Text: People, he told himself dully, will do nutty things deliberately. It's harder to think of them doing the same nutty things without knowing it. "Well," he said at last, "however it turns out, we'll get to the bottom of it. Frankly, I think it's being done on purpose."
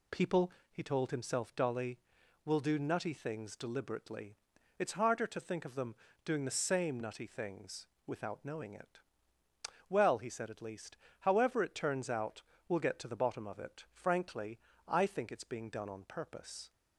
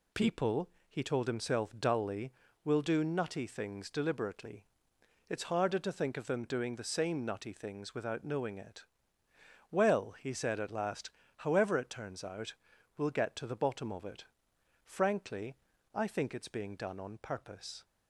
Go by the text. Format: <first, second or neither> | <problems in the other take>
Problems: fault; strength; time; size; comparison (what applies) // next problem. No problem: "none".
second | pauses between "them" and "doing"; slight; at 5.9 s; 0.30 s long // pauses between "things" and "without"; slight; at 7.8 s; 0.18 s long // says "least" for "last"; at 10.6 s